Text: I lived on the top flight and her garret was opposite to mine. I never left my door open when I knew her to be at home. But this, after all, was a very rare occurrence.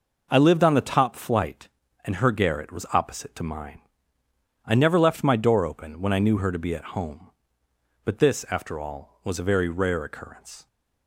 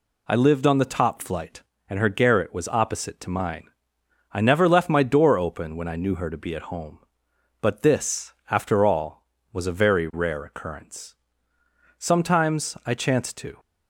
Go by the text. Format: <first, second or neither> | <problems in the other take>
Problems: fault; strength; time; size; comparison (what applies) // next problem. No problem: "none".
first | goes on to say "Sometimes I chanced to"; from 11.9 s on; 1.6 s long